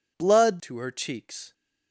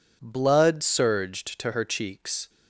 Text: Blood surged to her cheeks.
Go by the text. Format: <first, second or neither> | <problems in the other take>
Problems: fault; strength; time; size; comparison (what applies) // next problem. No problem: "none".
second | skips "surged"; at 0.6 s